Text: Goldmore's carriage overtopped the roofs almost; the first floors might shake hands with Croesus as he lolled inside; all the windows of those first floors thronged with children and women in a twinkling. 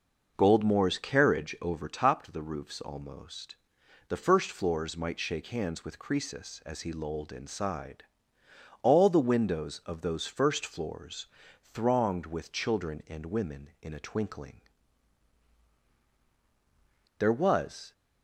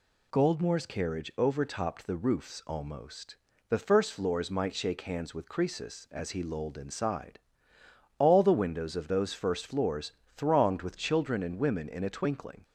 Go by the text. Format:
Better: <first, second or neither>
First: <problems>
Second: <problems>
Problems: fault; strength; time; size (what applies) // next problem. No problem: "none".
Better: second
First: pauses between "floors" and "thronged"; slight; at 11.2 s; 0.34 s long // goes on to say "There was"; noticeable; from 17.1 s on; 0.74 s long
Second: pauses between "floors" and "thronged"; slight; at 10.1 s; 0.24 s long